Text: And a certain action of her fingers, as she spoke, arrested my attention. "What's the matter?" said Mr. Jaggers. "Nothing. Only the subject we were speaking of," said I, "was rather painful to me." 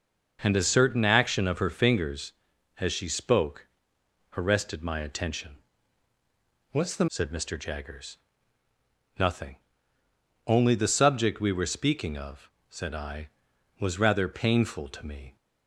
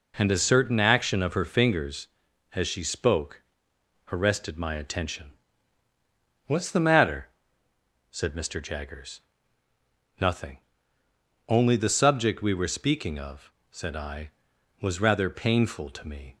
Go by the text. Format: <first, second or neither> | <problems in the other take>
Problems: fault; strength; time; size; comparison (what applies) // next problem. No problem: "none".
second | starts louder than the rest; until 1.4 s; 6 dB // skips "matter"; at 7.0 s